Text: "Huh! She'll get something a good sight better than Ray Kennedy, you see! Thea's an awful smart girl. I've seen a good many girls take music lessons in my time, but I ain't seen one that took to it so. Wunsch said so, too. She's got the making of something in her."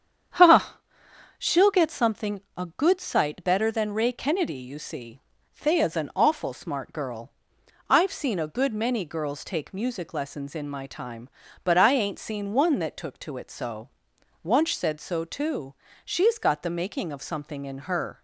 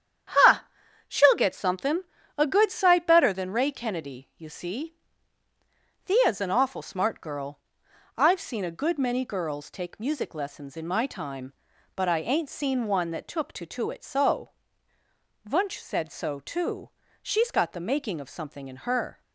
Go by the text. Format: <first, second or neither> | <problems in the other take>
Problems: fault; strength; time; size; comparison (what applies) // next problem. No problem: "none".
first | starts louder than the rest; strong; until 1.8 s; 9 dB; strong in the first // pauses between "something" and "a"; slight; at 2.0 s; 0.34 s long; slight in the first // says "to" twice; at 13.6 s